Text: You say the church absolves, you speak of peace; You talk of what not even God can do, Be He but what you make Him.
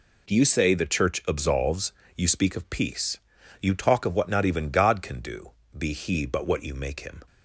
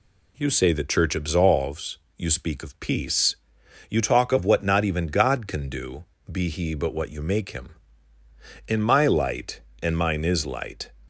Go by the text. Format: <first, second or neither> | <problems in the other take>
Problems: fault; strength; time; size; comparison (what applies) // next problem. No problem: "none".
first | goes on to say "In my light And mine is light"; strong; from 8.6 s on; 2.2 s long